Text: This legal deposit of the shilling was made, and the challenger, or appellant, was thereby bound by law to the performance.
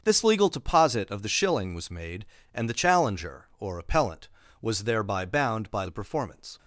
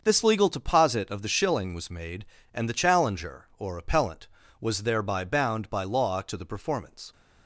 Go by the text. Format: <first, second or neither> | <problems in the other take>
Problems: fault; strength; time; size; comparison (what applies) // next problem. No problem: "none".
second | starts louder than the rest; until 1.0 s; 6.5 dB; also in the second // skips "law to"; at 5.8 s